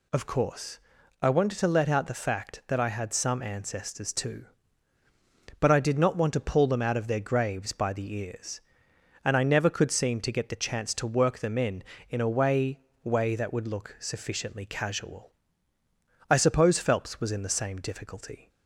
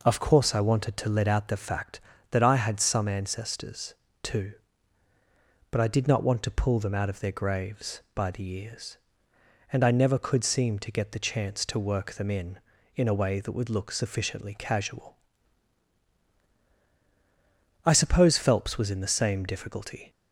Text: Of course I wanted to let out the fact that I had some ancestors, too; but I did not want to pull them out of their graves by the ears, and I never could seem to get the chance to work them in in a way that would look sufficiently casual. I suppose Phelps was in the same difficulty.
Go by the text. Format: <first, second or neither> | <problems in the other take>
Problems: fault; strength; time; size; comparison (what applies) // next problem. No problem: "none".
second | pauses between "course" and "I"; at 0.7 s; 0.42 s long // says "way" twice; at 13.0 s